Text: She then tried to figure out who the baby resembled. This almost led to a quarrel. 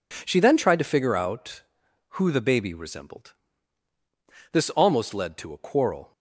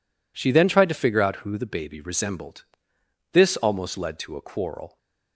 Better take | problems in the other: neither | none

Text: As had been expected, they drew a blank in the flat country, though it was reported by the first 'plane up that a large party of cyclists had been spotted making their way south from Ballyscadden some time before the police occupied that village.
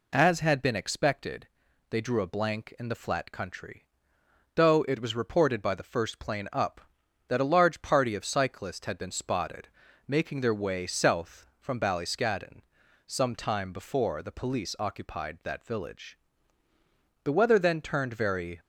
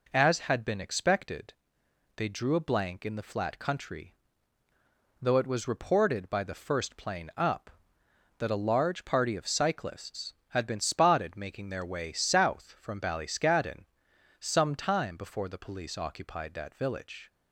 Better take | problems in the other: second | pauses between "spotted" and "making"; slight; at 9.6 s; 0.36 s long // pauses between "Ballyscadden" and "some"; noticeable; at 12.6 s; 0.46 s long; noticeable in the second // goes on to say "The weather then turned very"; from 17.2 s on; 1.3 s long

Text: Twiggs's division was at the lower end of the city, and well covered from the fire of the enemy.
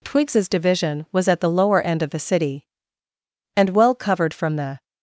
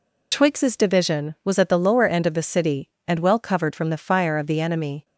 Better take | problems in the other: second | stops before "fire of the enemy"; at 4.8 s

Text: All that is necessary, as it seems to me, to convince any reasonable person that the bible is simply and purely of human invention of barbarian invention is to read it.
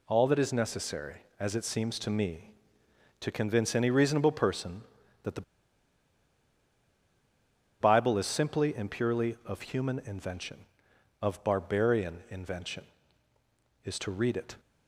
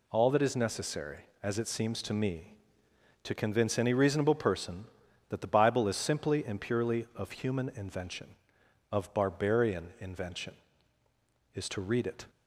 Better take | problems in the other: second | pauses between "the" and "bible"; strong; at 5.4 s; 2.3 s long

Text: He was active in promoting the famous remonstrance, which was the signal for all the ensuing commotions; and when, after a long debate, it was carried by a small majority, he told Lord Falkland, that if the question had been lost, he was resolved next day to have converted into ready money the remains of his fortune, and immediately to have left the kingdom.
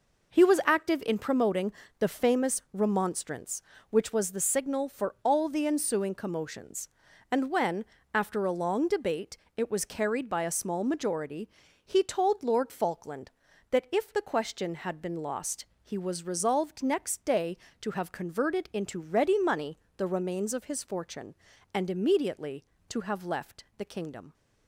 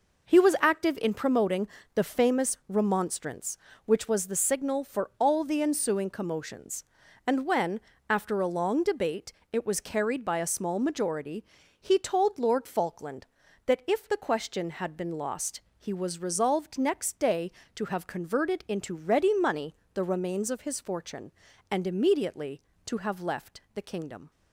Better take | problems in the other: neither | pauses between "promoting" and "the"; slight; the same in both // pauses between "money" and "the"; slight; the same in both

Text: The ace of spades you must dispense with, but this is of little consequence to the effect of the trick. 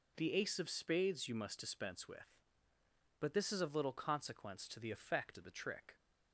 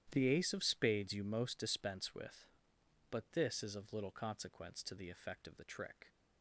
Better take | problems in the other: first | starts louder than the rest; strong; until 1.1 s; 11 dB // says "most" for "must"; at 1.2 s

